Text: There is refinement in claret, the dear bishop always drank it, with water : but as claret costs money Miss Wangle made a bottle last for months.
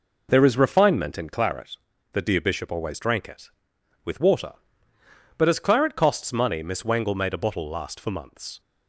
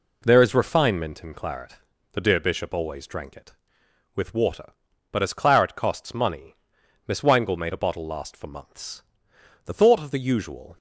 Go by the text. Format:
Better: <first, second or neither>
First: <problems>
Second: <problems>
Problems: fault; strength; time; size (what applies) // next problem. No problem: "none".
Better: first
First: none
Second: pauses between "money" and "Miss"; noticeable; at 6.5 s; 0.54 s long // goes on to say "The thought of the usual"; noticeable; from 9.6 s on; 1.1 s long